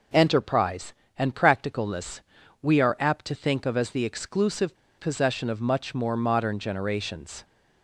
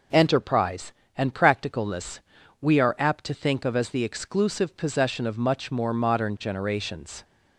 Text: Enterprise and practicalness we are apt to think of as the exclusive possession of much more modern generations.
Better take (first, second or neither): second